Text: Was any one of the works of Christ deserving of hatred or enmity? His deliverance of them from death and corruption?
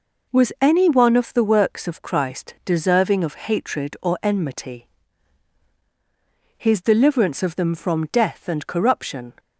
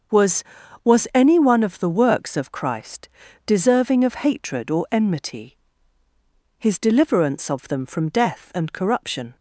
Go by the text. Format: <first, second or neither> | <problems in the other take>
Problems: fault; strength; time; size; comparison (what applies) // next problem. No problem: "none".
first | starts louder than the rest; until 1.6 s; 6.5 dB // says "Was" twice; at 0.8 s // pauses between "Christ" and "deserving"; at 3.0 s; 0.38 s long